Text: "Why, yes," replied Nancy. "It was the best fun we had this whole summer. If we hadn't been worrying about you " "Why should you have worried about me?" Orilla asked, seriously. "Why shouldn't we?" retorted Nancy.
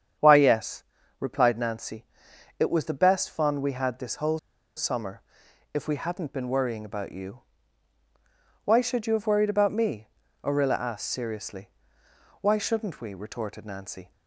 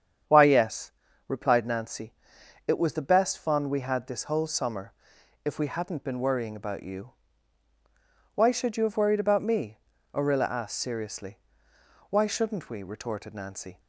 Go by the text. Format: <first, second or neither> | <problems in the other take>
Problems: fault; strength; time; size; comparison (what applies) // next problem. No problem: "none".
second | starts louder than the rest; strong; until 1.5 s; 8.5 dB; strong in the second // pauses between "whole" and "summer"; at 4.3 s; 0.38 s long